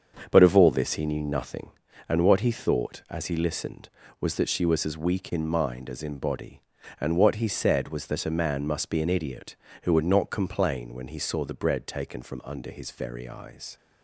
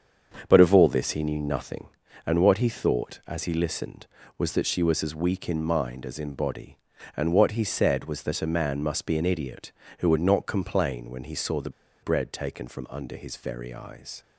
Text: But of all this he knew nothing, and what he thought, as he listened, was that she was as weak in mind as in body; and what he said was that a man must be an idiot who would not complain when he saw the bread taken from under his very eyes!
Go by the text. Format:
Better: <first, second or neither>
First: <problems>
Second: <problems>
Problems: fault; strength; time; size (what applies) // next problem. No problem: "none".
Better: first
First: starts louder than the rest; until 1.3 s; 7 dB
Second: starts louder than the rest; until 1.4 s; 7 dB // pauses between "the" and "bread"; slight; at 11.7 s; 0.32 s long